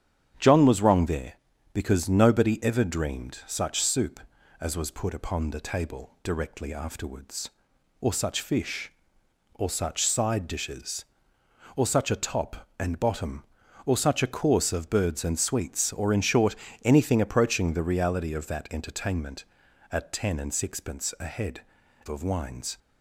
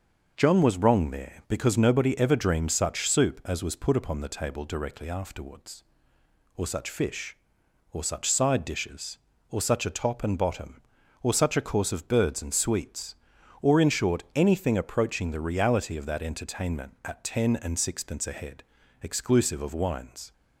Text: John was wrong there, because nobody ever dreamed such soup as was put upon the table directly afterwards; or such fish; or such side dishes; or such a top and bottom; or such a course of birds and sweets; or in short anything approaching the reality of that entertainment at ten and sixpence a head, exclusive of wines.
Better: second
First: starts louder than the rest; strong; until 1.7 s; 9 dB // pauses between "short" and "anything"; slight; at 16.5 s; 0.28 s long // skips "exclusive"; at 21.8 s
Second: none

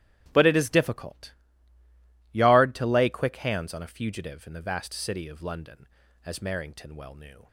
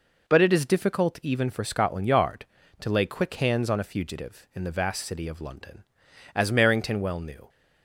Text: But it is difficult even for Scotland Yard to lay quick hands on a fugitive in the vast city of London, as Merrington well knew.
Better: second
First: starts louder than the rest; strong; until 1.3 s; 12.5 dB // skips "even for Scotland"; at 1.8 s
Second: none

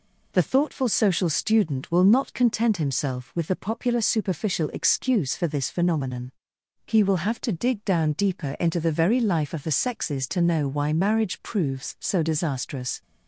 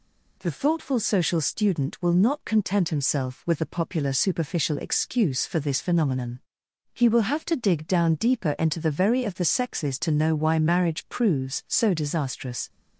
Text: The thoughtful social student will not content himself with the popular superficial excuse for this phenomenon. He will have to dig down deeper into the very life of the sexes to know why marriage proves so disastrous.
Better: first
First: none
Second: skips "life"; at 9.2 s

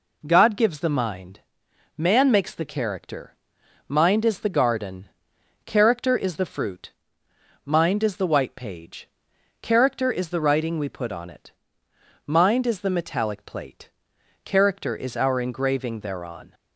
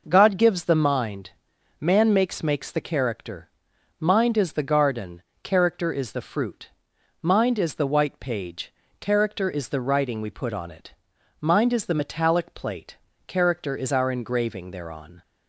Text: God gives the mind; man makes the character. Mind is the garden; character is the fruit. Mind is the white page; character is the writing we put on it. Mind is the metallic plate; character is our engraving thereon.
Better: first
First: none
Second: says "makes" twice; at 2.4 s

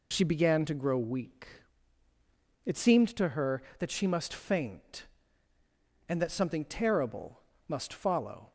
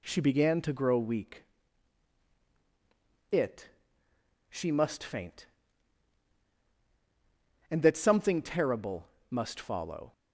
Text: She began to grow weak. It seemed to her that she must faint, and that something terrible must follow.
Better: first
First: pauses between "terrible" and "must"; slight; at 7.3 s; 0.26 s long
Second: skips "seemed to her that"; at 4.1 s // pauses between "terrible" and "must"; slight; at 9.0 s; 0.22 s long

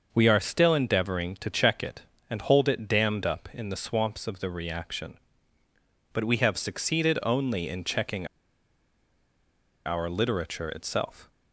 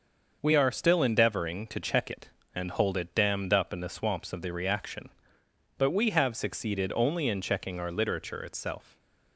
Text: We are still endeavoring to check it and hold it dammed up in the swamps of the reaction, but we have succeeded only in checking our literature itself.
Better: second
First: starts louder than the rest; until 1.1 s; 6.5 dB // pauses between "checking" and "our"; strong; at 8.2 s; 1.5 s long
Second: starts louder than the rest; until 1.4 s; 6 dB

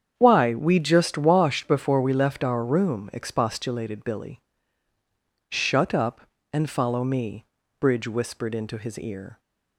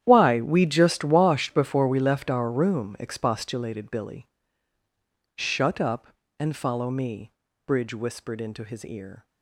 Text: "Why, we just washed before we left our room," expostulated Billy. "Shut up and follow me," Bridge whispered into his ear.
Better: first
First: starts louder than the rest; strong; until 1.1 s; 8 dB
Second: gets quieter; strong; throughout; 16 dB // starts louder than the rest; strong; until 1.0 s; 10.5 dB

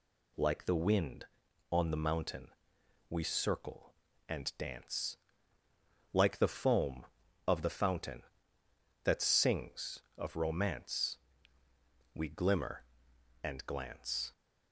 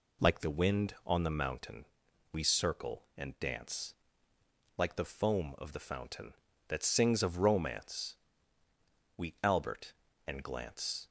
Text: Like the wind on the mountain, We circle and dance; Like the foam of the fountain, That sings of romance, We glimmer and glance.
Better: first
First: none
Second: says "albert" for "glimmer"; at 9.4 s

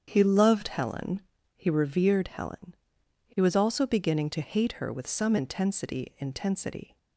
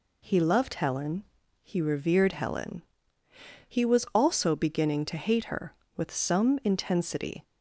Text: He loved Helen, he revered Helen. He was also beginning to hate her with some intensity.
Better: second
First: starts louder than the rest; strong; until 1.0 s; 8 dB // says "intensity" twice; at 6.1 s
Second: none

